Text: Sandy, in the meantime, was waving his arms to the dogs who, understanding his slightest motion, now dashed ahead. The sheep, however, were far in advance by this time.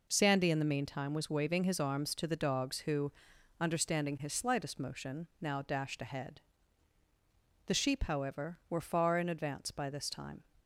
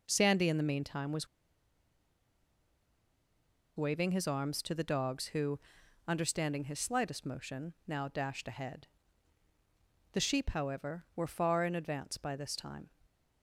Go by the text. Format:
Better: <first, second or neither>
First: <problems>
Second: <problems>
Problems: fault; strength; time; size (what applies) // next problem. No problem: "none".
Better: first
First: none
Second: pauses between "was" and "waving"; strong; at 1.2 s; 2.4 s long